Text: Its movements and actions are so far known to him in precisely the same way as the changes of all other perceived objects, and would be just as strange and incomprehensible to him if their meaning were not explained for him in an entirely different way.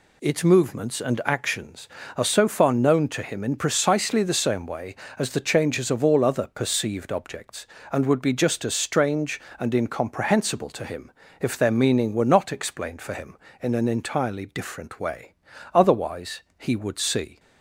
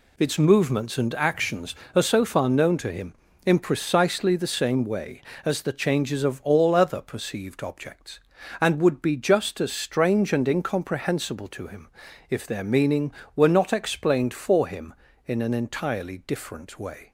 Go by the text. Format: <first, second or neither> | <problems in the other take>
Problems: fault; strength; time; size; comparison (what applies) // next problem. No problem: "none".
second | pauses between "him" and "if"; slight; at 11.0 s; 0.30 s long; also in the second // goes on to say "Otherwise he would see"; from 15.7 s on; 1.6 s long